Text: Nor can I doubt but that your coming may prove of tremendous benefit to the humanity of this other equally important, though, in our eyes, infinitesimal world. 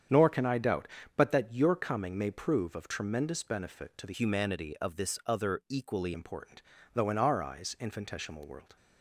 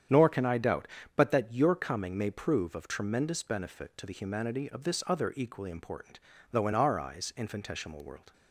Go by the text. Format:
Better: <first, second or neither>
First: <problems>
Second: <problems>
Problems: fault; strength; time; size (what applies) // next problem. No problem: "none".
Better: second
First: starts louder than the rest; strong; until 1.4 s; 8 dB // changes voice from "humanity" to "equally"; from 4.1 to 6.1 s; 2.0 s long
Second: starts louder than the rest; strong; until 1.3 s; 9 dB